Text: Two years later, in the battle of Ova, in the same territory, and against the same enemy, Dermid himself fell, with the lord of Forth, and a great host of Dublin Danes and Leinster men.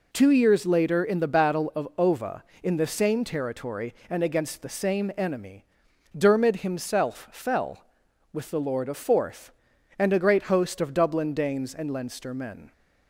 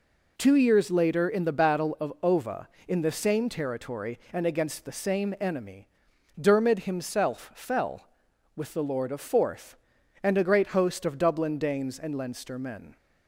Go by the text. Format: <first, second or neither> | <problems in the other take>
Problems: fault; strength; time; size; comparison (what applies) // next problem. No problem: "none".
neither | none